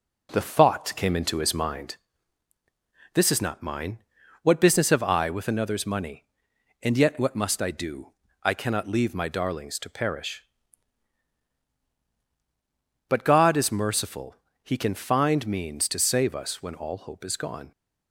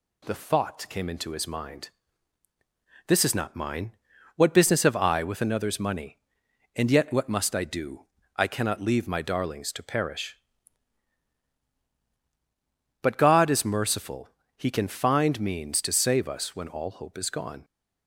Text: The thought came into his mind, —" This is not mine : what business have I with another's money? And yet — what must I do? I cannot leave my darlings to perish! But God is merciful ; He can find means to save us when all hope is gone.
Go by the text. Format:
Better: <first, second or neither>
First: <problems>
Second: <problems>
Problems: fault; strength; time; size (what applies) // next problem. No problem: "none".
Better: second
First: starts louder than the rest; noticeable; until 2.1 s; 4 dB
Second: none